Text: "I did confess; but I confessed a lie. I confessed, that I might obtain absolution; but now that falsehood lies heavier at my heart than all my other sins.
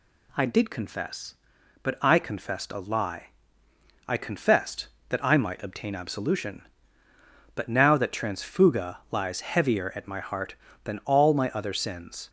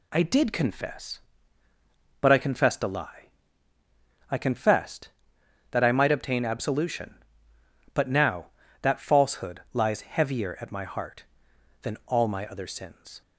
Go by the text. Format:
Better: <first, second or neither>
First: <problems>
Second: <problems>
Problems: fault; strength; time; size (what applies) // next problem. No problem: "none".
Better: second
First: says "transfuga" for "falsehood"; at 8.1 s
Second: none